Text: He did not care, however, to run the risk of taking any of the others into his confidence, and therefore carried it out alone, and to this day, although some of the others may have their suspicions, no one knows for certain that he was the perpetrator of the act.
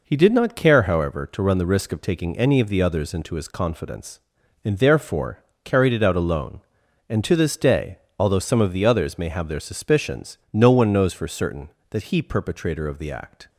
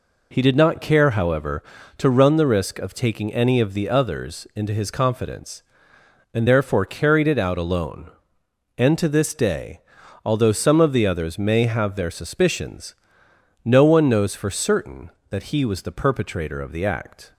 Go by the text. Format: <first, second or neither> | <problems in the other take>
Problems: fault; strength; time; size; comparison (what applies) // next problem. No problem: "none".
second | pauses between "therefore" and "carried"; slight; at 5.4 s; 0.22 s long // skips "was the"; at 12.2 s